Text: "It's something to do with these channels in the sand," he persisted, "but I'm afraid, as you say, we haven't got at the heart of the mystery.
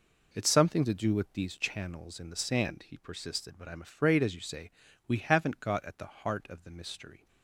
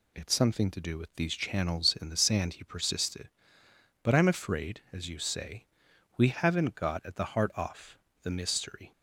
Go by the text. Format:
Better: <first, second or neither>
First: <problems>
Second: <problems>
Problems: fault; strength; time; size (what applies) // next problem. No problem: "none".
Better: first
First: none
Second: says "off" for "of"; at 7.5 s